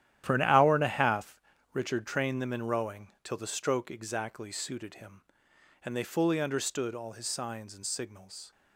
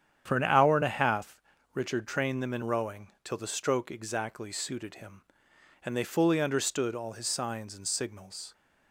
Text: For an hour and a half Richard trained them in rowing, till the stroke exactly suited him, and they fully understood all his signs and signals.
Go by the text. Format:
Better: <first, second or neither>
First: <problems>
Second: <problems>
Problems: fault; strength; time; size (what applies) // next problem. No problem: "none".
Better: second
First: gets quieter; strong; throughout; 12 dB // starts louder than the rest; strong; until 1.2 s; 12 dB // pauses between "half" and "Richard"; at 1.3 s; 0.38 s long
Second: starts louder than the rest; strong; until 1.2 s; 9 dB // pauses between "half" and "Richard"; at 1.3 s; 0.38 s long